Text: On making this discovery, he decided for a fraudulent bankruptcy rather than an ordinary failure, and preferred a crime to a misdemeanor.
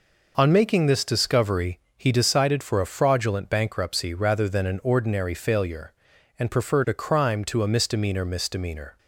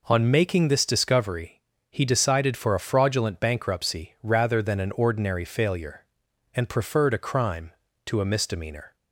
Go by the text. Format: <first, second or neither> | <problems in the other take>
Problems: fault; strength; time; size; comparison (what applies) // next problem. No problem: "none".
second | says "misdemeanor" twice; at 8.2 s